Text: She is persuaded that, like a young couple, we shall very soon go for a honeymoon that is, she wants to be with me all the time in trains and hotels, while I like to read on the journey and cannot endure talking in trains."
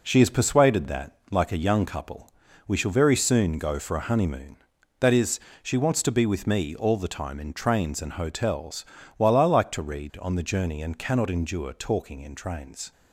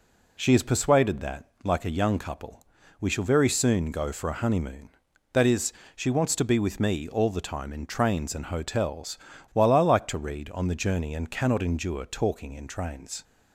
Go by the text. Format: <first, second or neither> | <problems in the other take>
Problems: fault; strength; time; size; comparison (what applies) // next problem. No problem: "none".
second | gets quieter; throughout; 6.5 dB